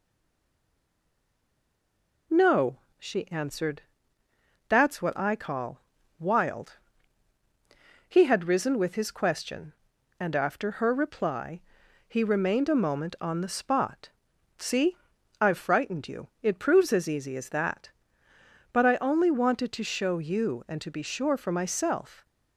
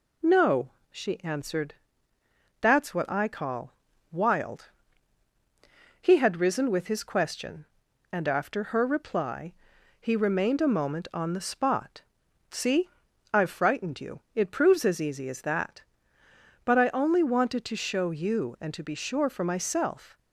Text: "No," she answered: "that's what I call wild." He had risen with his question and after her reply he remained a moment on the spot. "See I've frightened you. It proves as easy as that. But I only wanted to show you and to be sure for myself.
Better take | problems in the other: second | stays silent before the first word; until 2.3 s; 2.3 s long // pauses between "call" and "wild"; at 5.8 s; 0.38 s long; also in the second // pauses between "reply" and "he"; noticeable; at 11.6 s; 0.46 s long; noticeable in the second // pauses between "See" and "I've"; at 14.9 s; 0.42 s long; also in the second

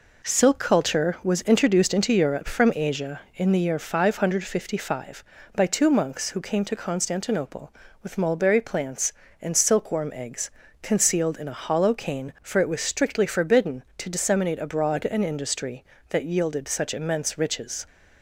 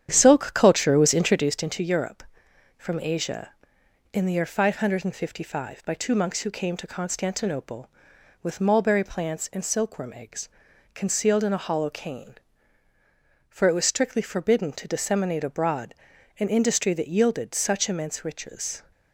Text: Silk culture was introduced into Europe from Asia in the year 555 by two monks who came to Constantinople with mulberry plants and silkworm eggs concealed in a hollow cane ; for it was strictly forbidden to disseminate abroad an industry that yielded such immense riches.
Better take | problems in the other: first | starts louder than the rest; strong; until 1.5 s; 9.5 dB // pauses between "eggs" and "concealed"; noticeable; at 10.4 s; 0.48 s long; slight in the first // pauses between "abroad" and "an"; noticeable; at 15.9 s; 0.46 s long

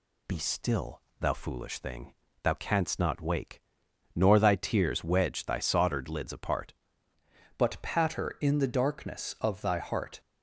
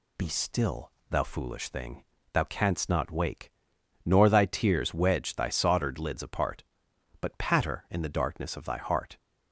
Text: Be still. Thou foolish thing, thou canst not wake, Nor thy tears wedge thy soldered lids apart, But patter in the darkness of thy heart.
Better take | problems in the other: second | changes voice at "But"; from 7.5 s on; 2.6 s long

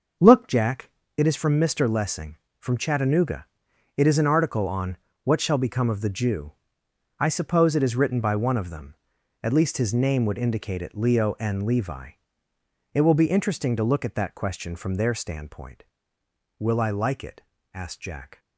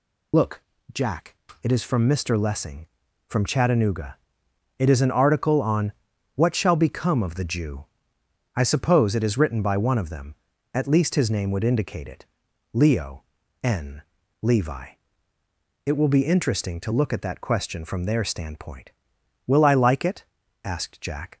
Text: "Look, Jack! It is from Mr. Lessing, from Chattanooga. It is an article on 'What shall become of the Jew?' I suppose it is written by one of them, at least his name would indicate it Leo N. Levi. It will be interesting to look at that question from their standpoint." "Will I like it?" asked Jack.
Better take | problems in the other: first | loses the start of "Look"; at 0.3 s; 75 ms // pauses between "on" and "What"; at 5.9 s; 0.42 s long; slight in the first // pauses between "it" and "Leo"; noticeable; at 12.2 s; 0.48 s long // pauses between "Leo" and "N"; at 13.2 s; 0.40 s long

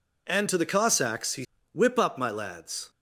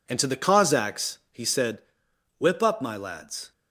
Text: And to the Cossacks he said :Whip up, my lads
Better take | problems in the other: second | skips "said"; at 1.5 s

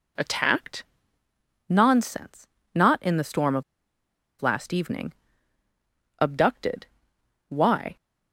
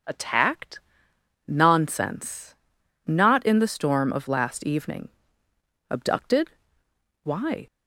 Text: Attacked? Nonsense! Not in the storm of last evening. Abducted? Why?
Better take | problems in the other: second | pauses between "of" and "last"; noticeable; at 3.6 s; 0.78 s long

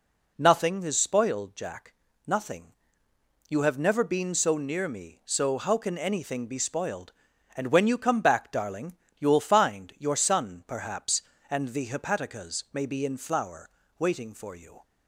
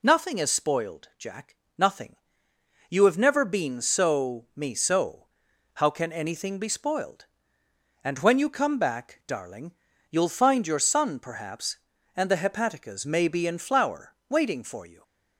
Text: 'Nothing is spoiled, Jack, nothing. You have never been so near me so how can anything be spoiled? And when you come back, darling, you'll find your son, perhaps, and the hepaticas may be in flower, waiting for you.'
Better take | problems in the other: first | skips "near"; at 4.4 s // pauses between "so" and "how"; noticeable; at 5.2 s; 0.52 s long

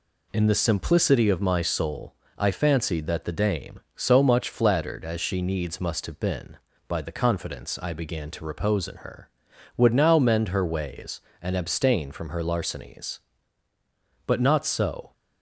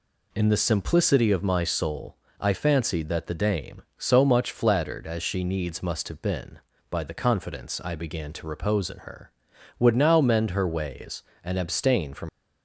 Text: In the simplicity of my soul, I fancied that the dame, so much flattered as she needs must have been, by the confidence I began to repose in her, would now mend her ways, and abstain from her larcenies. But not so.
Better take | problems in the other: first | stops before "her larcenies But not so"; at 12.2 s

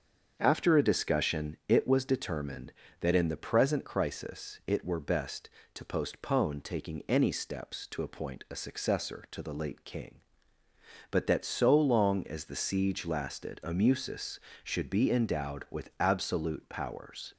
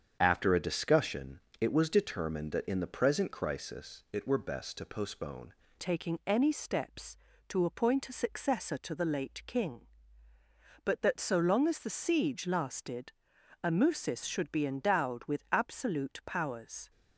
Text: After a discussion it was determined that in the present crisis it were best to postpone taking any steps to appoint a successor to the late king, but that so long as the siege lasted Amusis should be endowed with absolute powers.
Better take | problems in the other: first | starts louder than the rest; strong; until 1.2 s; 7.5 dB; strong in the first // pauses between "discussion" and "it"; slight; at 1.4 s; 0.20 s long // changes voice at "taking"; from 5.8 s on; 11.0 s long // pauses between "lasted" and "Amusis"; noticeable; at 13.1 s; 0.50 s long

